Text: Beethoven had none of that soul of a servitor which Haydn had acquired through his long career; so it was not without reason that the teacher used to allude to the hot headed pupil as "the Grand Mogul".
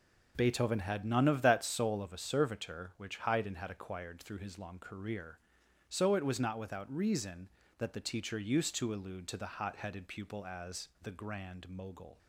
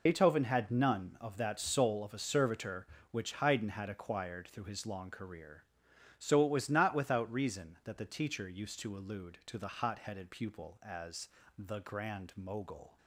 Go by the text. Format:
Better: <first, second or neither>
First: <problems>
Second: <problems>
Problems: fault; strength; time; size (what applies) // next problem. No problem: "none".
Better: first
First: none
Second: loses the start of "Beethoven"; at 0.0 s; 85 ms // pauses between "as" and "the"; slight; at 11.2 s; 0.28 s long